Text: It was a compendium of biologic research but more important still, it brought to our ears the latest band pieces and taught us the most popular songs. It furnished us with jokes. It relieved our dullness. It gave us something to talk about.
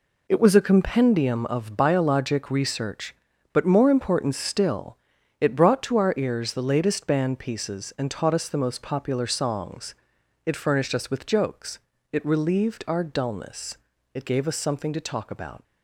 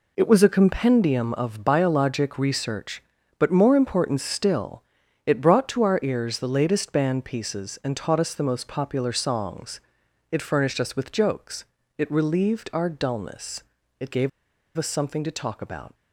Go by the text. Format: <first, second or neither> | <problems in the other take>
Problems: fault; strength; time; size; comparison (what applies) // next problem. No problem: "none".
first | pauses between "gave" and "us"; noticeable; at 14.2 s; 0.48 s long